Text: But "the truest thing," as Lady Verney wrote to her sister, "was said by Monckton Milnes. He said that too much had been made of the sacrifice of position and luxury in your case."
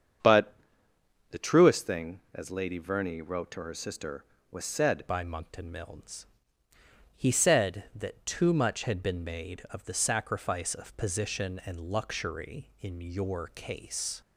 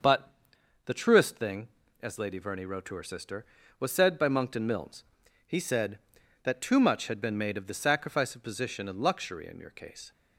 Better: second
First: starts louder than the rest; strong; until 2.0 s; 7.5 dB // pauses between "But" and "the"; noticeable; at 0.5 s; 0.78 s long // changes voice at "by"; from 5.0 s on; 9.2 s long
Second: starts louder than the rest; until 1.5 s; 6 dB // pauses between "But" and "the"; noticeable; at 0.3 s; 0.54 s long

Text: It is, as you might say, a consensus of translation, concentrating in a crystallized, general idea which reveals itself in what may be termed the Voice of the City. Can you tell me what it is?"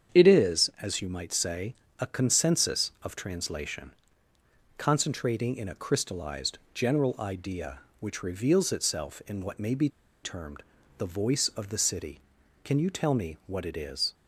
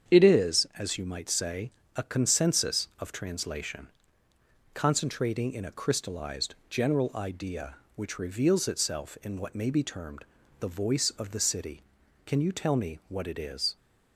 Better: second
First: starts louder than the rest; strong; until 1.2 s; 8 dB // pauses between "be" and "termed"; slight; at 9.8 s; 0.33 s long // pauses between "termed" and "the"; slight; at 10.6 s; 0.34 s long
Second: starts louder than the rest; strong; until 1.1 s; 8 dB // pauses between "termed" and "the"; slight; at 10.2 s; 0.34 s long

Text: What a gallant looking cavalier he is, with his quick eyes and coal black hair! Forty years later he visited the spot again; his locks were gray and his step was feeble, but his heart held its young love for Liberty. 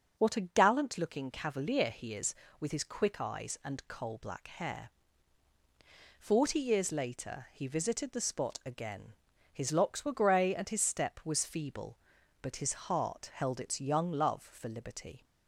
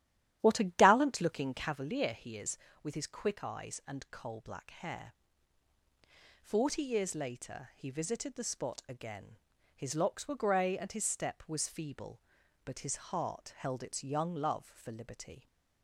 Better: first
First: none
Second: starts louder than the rest; strong; until 1.8 s; 11.5 dB

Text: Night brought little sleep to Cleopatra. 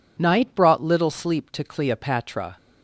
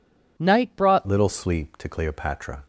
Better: first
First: none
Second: changes voice at "little"; from 1.0 s on; 1.6 s long

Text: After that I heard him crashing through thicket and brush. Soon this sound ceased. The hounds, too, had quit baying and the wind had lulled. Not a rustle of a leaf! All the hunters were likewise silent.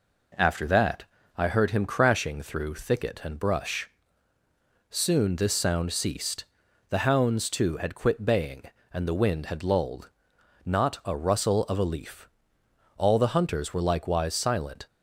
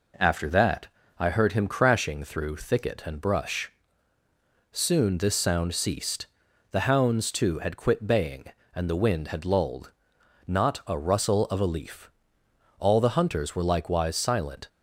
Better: neither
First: pauses between "that" and "I"; slight; at 1.0 s; 0.32 s long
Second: pauses between "that" and "I"; slight; at 0.8 s; 0.30 s long

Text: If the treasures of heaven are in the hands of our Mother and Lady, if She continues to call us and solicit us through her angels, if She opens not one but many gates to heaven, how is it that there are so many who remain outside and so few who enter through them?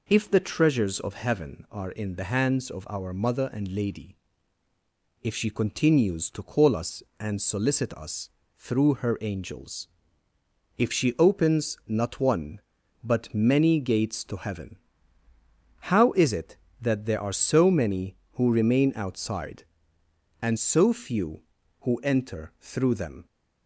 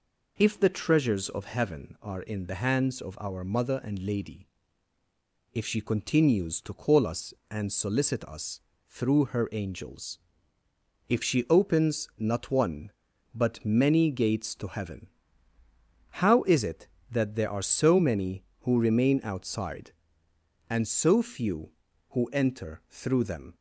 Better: neither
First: pauses between "us" and "through"; slight; at 8.2 s; 0.28 s long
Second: pauses between "us" and "through"; slight; at 8.5 s; 0.28 s long

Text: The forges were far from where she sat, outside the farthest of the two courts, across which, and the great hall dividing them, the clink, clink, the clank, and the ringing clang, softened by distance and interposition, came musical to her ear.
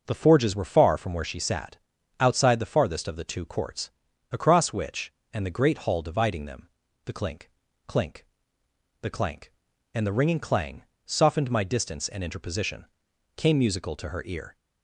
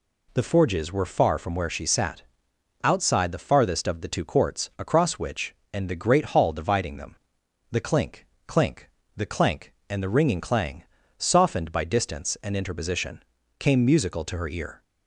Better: second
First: starts louder than the rest; noticeable; until 1.0 s; 6 dB // says "my" for "by"; at 11.4 s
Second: none

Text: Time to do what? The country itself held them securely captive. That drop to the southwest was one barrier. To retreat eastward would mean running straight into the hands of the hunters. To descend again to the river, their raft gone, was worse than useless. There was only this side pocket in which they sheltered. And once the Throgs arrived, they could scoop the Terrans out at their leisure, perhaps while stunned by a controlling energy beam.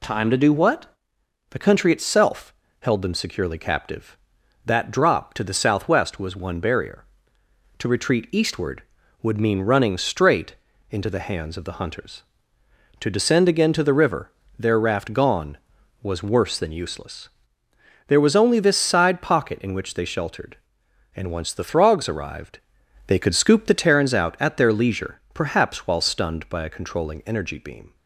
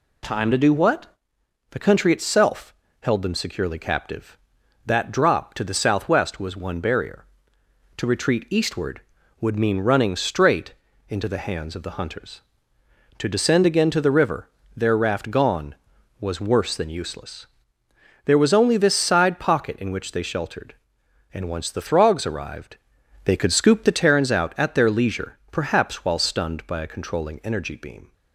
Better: neither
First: pauses between "itself" and "held"; slight; at 2.5 s; 0.28 s long // pauses between "straight" and "into"; slight; at 10.5 s; 0.34 s long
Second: pauses between "itself" and "held"; slight; at 2.7 s; 0.28 s long // pauses between "straight" and "into"; slight; at 10.7 s; 0.34 s long

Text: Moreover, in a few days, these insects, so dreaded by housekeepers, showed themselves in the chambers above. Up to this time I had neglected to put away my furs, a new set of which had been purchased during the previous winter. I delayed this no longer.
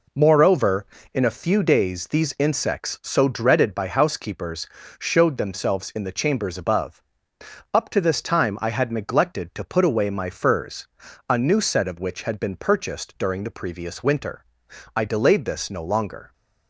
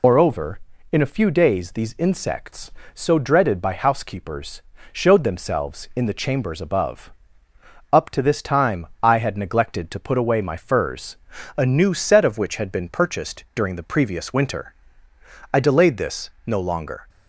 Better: first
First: none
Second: loses the start of "Moreover"; at 0.0 s; 105 ms // pauses between "time" and "I"; slight; at 8.8 s; 0.16 s long

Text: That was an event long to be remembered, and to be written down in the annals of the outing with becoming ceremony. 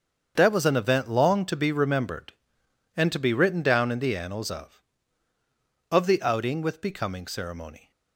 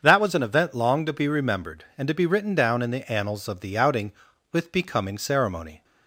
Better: second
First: starts louder than the rest; strong; until 1.3 s; 7 dB // says "of" twice; at 5.9 s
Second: starts louder than the rest; until 1.0 s; 7 dB

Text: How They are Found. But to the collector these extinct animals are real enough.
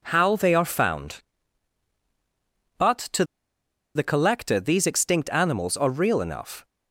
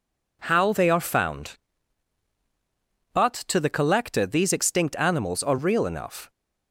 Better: second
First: pauses between "to" and "the"; noticeable; at 3.2 s; 0.71 s long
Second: none

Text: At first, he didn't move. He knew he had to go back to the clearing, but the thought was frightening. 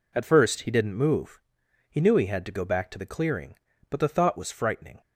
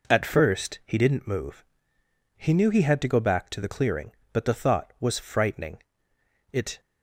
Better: first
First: none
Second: goes on to say "It"; slight; from 6.5 s on; 0.28 s long

